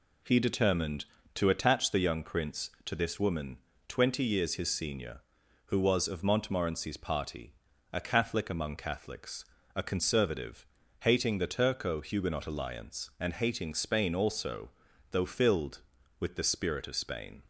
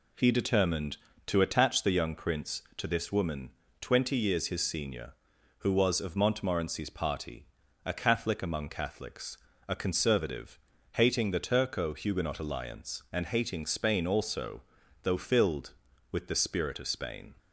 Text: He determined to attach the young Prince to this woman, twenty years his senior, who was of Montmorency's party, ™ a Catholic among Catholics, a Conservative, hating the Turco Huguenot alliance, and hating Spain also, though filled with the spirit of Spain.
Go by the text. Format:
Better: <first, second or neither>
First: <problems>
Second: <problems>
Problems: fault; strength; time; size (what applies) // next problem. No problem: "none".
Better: neither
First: none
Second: none